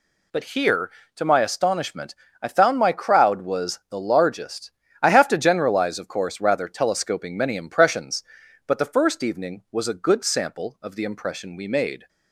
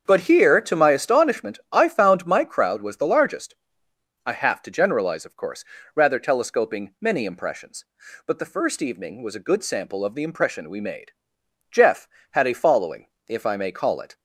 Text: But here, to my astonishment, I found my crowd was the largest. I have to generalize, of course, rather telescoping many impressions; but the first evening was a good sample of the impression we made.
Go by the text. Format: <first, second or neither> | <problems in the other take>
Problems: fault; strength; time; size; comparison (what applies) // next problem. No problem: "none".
first | starts louder than the rest; strong; until 1.0 s; 7.5 dB // goes on to say "Jeff had a following if I may call it"; strong; from 11.7 s on; 2.4 s long